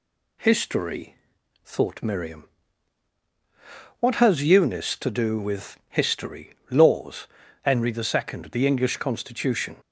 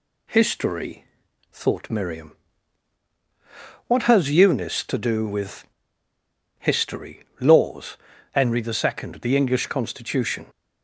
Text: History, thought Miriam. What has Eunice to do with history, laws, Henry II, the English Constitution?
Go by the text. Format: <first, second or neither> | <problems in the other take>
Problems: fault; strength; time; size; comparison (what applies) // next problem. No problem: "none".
first | pauses between "with" and "history"; noticeable; at 5.6 s; 0.94 s long